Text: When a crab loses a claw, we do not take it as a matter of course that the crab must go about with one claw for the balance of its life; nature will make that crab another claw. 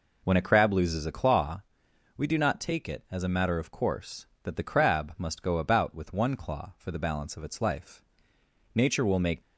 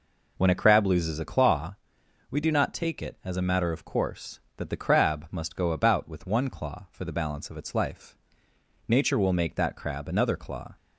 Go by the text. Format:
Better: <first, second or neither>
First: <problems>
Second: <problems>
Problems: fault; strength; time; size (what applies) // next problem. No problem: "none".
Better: second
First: stops before "that crab another claw"; at 9.4 s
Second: none